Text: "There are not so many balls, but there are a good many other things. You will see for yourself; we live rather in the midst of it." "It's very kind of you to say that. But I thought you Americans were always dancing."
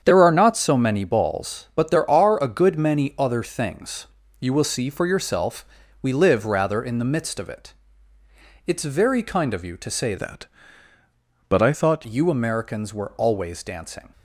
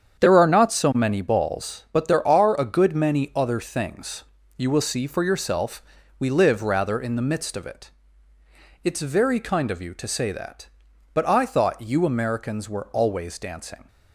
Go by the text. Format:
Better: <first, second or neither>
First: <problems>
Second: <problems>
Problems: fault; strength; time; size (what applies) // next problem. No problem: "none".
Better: second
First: starts louder than the rest; strong; until 1.0 s; 8 dB // changes voice from "that" to "thought"; from 10.1 to 12.0 s; 1.9 s long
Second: starts louder than the rest; strong; until 1.2 s; 8 dB